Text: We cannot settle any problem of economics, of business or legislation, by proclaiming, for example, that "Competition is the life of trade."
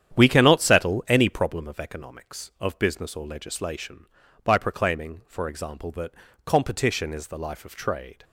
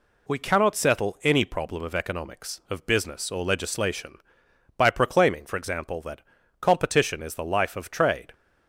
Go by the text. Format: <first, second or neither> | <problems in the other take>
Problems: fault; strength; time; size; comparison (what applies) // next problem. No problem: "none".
second | starts louder than the rest; strong; until 1.6 s; 9.5 dB // pauses between "that" and "Competition"; slight; at 6.1 s; 0.34 s long; also in the second